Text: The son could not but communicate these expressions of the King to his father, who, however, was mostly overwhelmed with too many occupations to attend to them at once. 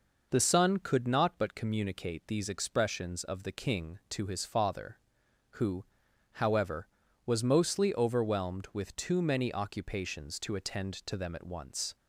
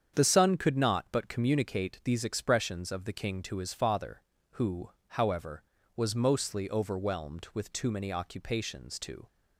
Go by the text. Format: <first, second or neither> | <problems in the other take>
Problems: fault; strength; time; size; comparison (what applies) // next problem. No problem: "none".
first | starts louder than the rest; strong; until 1.1 s; 8 dB // stops before "attend to them at once"; at 9.2 s